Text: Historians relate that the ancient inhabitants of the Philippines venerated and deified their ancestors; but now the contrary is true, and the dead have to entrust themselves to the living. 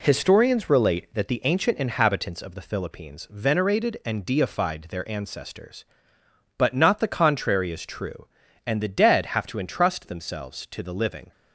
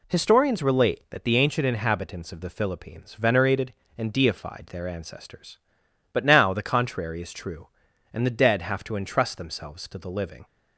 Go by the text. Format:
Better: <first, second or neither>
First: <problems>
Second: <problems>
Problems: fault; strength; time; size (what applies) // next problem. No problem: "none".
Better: second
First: says "not" for "now"; at 6.7 s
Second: none